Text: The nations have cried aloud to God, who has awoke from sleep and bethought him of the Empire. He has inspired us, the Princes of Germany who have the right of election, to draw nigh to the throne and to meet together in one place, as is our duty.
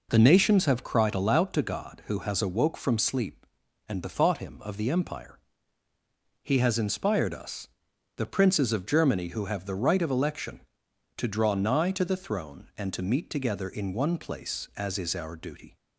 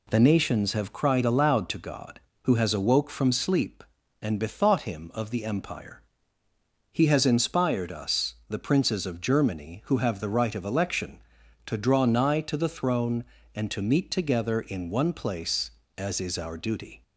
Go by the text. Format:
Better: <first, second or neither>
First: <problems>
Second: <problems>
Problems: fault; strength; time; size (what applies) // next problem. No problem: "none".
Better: neither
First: none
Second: none